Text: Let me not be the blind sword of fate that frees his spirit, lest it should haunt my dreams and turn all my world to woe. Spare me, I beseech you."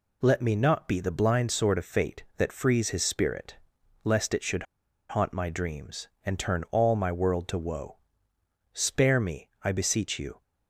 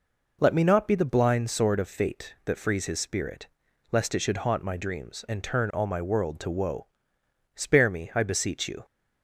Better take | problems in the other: second | pauses between "should" and "haunt"; at 4.6 s; 0.44 s long

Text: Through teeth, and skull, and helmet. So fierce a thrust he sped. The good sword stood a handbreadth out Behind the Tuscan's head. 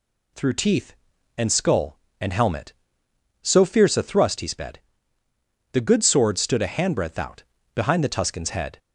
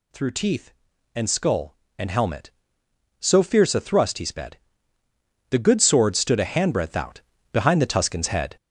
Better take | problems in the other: first | gets louder; throughout; 6.5 dB // pauses between "out" and "Behind"; slight; at 7.2 s; 0.30 s long; slight in the first

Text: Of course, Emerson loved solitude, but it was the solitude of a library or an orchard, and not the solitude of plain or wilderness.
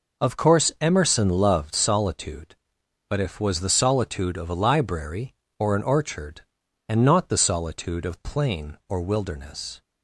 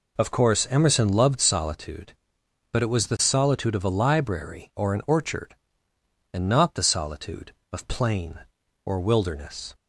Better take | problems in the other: second | says "if" for "it"; at 3.1 s

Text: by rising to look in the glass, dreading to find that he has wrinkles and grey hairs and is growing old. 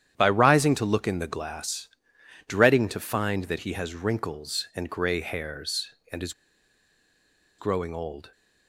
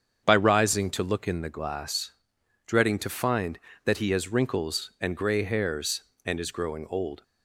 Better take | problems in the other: second | starts louder than the rest; strong; until 1.1 s; 10 dB; strong in the second // pauses between "is" and "growing"; strong; at 6.3 s; 1.2 s long

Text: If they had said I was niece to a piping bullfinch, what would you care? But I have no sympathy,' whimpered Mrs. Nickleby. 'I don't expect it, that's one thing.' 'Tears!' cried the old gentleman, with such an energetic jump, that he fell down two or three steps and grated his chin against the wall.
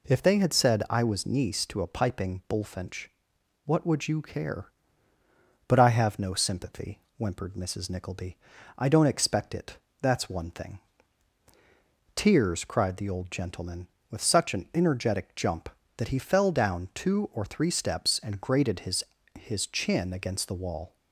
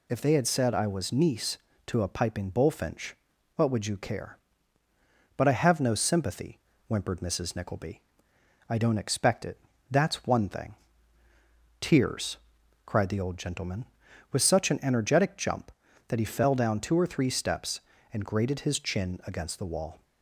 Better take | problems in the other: second | says "his" twice; at 19.3 s

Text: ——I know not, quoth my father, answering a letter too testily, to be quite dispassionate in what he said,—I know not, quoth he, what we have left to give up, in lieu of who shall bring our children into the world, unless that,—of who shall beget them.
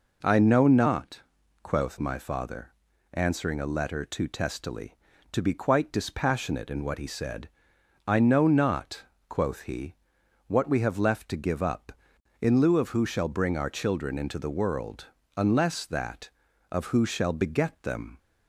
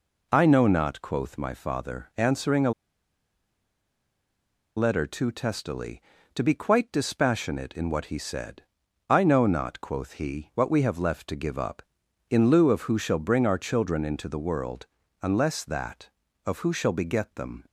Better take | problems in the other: first | pauses between "a" and "letter"; strong; at 2.7 s; 2.0 s long

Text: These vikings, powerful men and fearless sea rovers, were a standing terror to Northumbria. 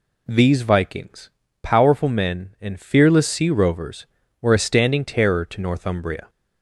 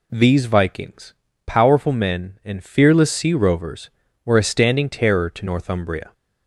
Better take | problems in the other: neither | none

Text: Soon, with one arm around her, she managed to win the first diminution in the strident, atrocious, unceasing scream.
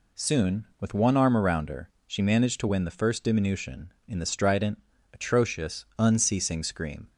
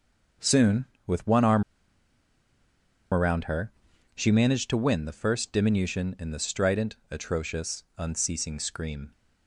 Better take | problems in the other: first | starts louder than the rest; until 1.6 s; 6.5 dB // pauses between "arm" and "around"; strong; at 1.6 s; 1.5 s long

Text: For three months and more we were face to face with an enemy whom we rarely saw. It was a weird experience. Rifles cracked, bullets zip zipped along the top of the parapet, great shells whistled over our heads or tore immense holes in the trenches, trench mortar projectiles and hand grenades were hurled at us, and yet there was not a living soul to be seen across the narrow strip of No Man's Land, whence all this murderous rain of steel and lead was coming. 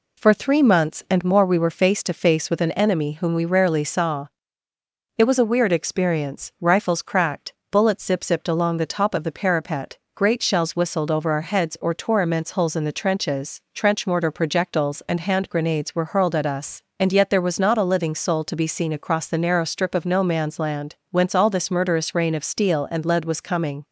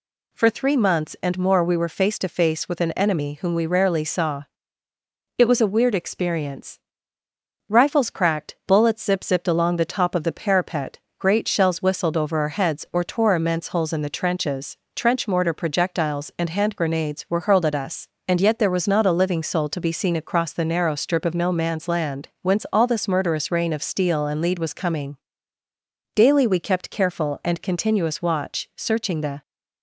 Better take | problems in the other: first | goes on to say "Daily we kept careful and continuous watch searching the"; strong; from 26.1 s on; 3.2 s long

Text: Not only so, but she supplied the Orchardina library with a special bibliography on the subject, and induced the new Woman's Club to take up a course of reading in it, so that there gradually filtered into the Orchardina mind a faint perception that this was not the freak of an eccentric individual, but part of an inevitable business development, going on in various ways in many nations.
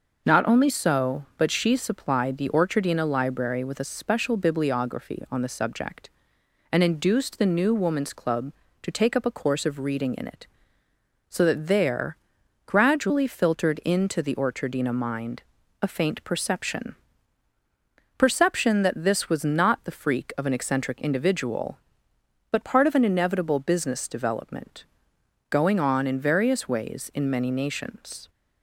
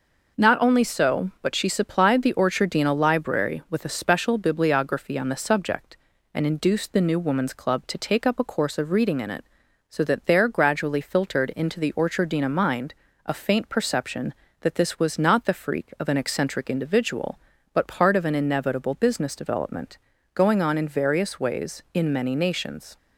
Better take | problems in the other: second | pauses between "there" and "gradually"; noticeable; at 12.1 s; 0.48 s long // pauses between "mind" and "a"; at 15.4 s; 0.40 s long; slight in the second // says "perception" twice; at 18.1 s

